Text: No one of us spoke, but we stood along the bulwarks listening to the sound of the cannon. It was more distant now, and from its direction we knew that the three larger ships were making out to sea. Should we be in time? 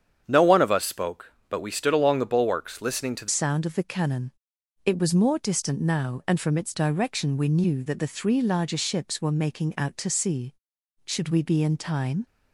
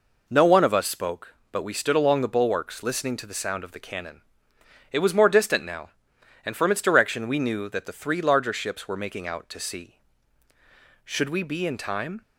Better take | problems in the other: second | starts louder than the rest; strong; until 1.2 s; 8.5 dB // changes voice at "sound"; from 3.2 s on; 9.0 s long

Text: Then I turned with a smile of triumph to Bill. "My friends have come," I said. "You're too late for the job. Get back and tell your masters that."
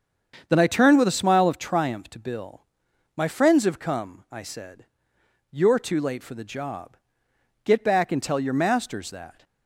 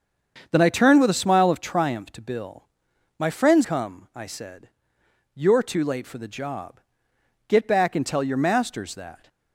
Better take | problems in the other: first | starts louder than the rest; strong; until 1.5 s; 7 dB; strong in the first // skips "have"; at 3.6 s

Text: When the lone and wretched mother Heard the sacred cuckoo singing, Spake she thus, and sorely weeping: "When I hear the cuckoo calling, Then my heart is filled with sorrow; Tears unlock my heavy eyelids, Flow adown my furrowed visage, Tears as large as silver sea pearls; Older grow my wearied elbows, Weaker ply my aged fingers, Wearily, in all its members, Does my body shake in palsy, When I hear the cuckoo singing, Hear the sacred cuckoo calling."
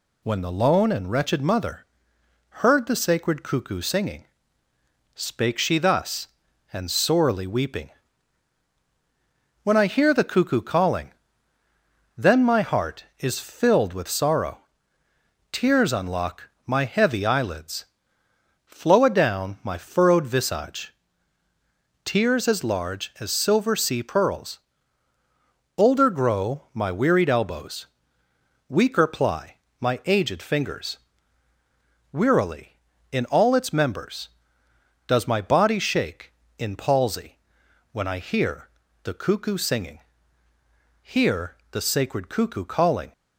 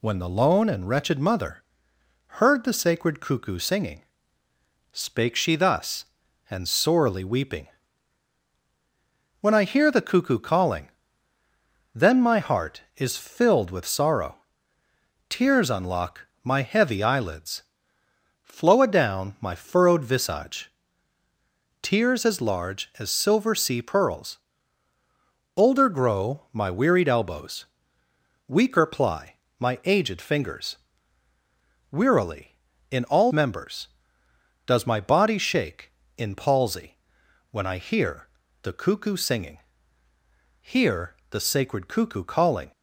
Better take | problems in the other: first | pauses between "mother" and "Heard"; noticeable; at 1.6 s; 0.74 s long; noticeable in the first // pauses between "unlock" and "my"; slight; at 16.2 s; 0.18 s long; slight in the first // pauses between "ply" and "my"; slight; at 29.3 s; 0.24 s long; slight in the first // skips "its"; at 33.3 s // pauses between "hear" and "the"; slight; at 38.2 s; 0.34 s long; slight in the first // pauses between "Hear" and "the"; slight; at 41.1 s; 0.16 s long; slight in the first

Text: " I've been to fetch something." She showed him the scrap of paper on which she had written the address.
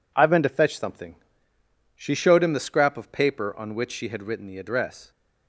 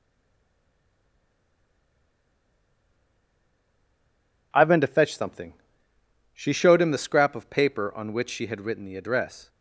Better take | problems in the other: first | stays silent before the first word; strong; until 4.5 s; 4.5 s long

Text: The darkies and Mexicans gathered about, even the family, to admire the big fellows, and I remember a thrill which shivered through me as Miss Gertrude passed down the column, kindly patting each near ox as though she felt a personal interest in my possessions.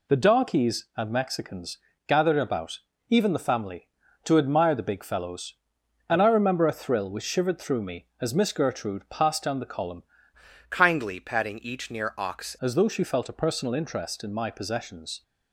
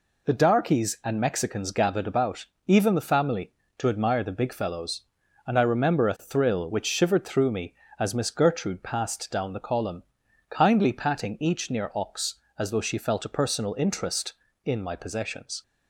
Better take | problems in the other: second | pauses between "Mexicans" and "gathered"; slight; at 1.7 s; 0.28 s long // changes voice from "kindly" to "ox"; from 10.7 to 12.5 s; 1.8 s long

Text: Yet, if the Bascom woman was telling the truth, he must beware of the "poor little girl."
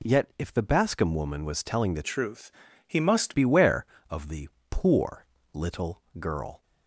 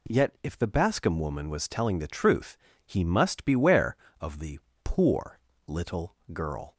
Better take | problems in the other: second | changes voice from "truth" to "must"; from 2.0 to 3.3 s; 1.3 s long // pauses between "the" and "poor"; slight; at 4.4 s; 0.20 s long; slight in the second // pauses between "poor" and "little"; slight; at 5.2 s; 0.30 s long; slight in the second // pauses between "little" and "girl"; slight; at 6.0 s; 0.16 s long; slight in the second

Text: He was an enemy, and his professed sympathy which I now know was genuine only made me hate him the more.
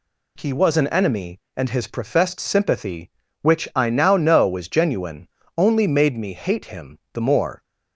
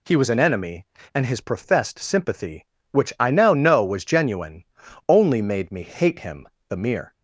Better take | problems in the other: first | pauses between "genuine" and "only"; at 4.6 s; 0.42 s long; slight in the first // pauses between "him" and "the"; slight; at 6.4 s; 0.22 s long // says "mere" for "more"; at 6.7 s

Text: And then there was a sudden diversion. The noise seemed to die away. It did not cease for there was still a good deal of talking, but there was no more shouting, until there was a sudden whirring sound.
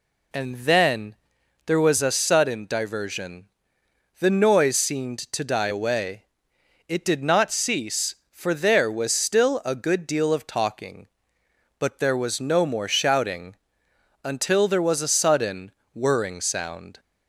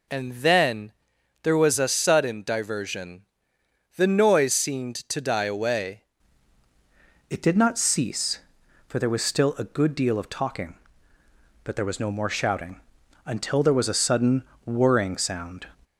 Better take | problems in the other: first | pauses between "then" and "there"; noticeable; at 0.9 s; 0.50 s long; noticeable in the first // changes voice at "It"; from 7.2 s on; 8.4 s long // pauses between "sudden" and "whirring"; slight; at 14.4 s; 0.22 s long; slight in the first

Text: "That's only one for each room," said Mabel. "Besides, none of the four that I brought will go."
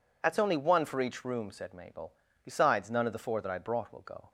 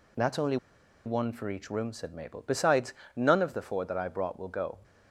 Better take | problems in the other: first | pauses between "only" and "one"; noticeable; at 0.5 s; 0.49 s long

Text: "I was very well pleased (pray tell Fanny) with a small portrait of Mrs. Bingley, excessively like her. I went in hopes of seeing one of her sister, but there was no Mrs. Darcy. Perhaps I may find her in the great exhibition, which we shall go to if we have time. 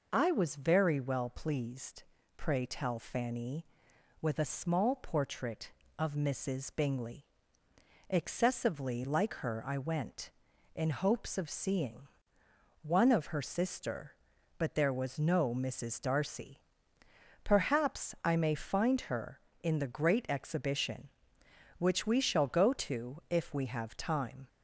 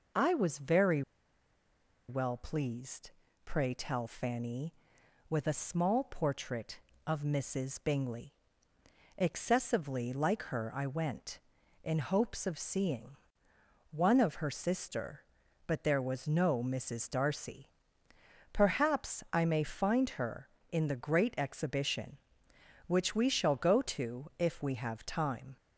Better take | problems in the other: first | pauses between "very" and "well"; at 1.0 s; 1.0 s long // pauses between "seeing" and "one"; noticeable; at 13.1 s; 0.74 s long; noticeable in the first

